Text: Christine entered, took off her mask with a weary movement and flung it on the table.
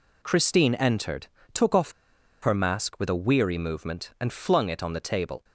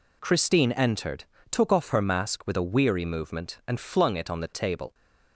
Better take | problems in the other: second | pauses between "off" and "her"; noticeable; at 1.9 s; 0.50 s long

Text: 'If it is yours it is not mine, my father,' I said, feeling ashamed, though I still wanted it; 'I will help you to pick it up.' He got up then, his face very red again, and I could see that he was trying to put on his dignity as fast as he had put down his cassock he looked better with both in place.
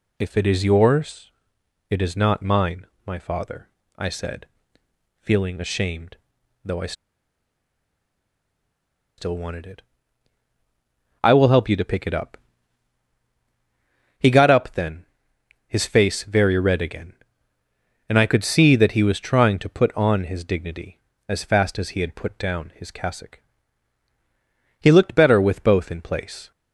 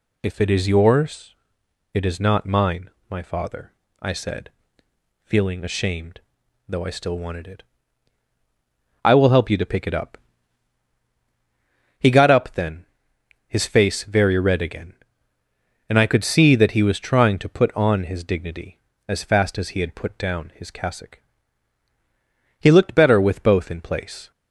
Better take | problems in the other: second | pauses between "yours" and "it"; noticeable; at 1.3 s; 0.58 s long; noticeable in the second // pauses between "I" and "still"; strong; at 6.9 s; 2.2 s long // pauses between "cassock" and "he"; strong; at 23.4 s; 1.4 s long; strong in the second

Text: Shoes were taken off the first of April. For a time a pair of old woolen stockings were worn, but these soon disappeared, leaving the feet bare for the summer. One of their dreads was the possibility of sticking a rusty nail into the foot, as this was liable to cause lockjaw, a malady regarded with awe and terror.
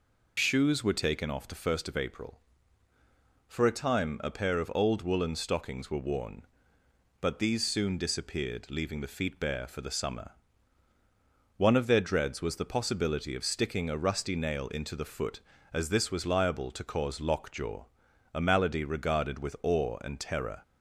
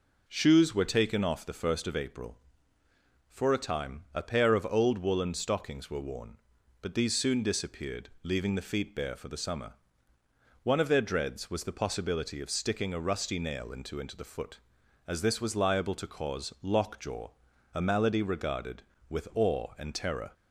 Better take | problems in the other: first | says "into" twice; at 14.0 s

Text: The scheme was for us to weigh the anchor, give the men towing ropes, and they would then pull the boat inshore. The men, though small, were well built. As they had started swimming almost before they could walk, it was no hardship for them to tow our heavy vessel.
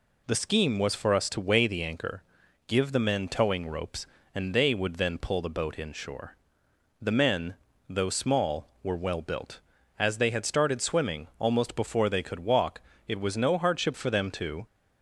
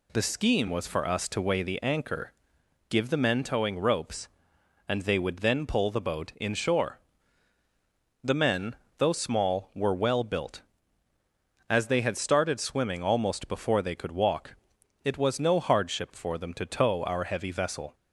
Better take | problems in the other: second | stops before "tow our heavy vessel"; at 14.6 s

